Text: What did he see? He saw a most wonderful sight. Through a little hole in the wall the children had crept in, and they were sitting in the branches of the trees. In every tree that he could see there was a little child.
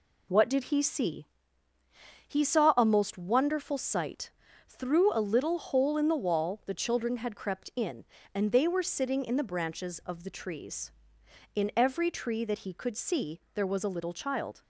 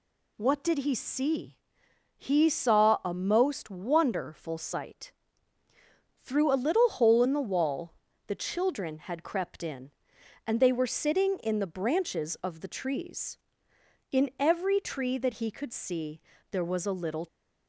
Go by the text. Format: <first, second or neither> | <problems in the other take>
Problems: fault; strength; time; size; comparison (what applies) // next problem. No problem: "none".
first | pauses between "wall" and "the"; slight; at 7.9 s; 0.33 s long // pauses between "see" and "there"; slight; at 16.1 s; 0.32 s long // stops before "child"; at 17.2 s